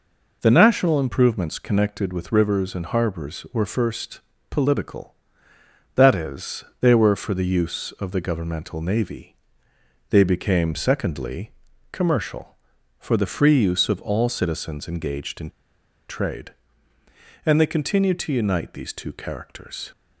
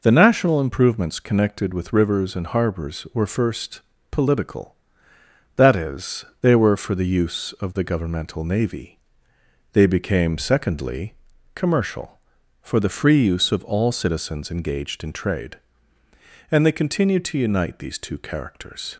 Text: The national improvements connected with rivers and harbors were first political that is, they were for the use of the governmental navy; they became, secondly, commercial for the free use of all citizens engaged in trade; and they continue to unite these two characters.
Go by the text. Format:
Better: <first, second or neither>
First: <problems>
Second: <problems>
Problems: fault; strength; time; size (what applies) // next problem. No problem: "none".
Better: second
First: pauses between "first" and "political"; slight; at 4.1 s; 0.32 s long // pauses between "in" and "trade"; noticeable; at 15.4 s; 0.59 s long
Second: pauses between "first" and "political"; slight; at 3.8 s; 0.32 s long